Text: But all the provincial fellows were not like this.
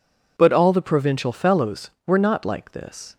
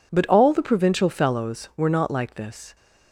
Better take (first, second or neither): neither